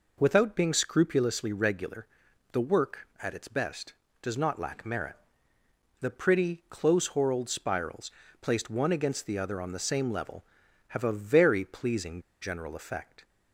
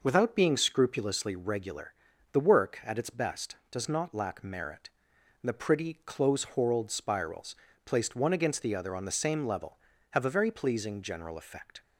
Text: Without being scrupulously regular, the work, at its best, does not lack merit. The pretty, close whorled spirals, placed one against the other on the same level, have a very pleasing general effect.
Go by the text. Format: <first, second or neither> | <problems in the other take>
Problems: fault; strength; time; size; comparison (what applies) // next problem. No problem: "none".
second | pauses between "pleasing" and "general"; slight; at 12.2 s; 0.20 s long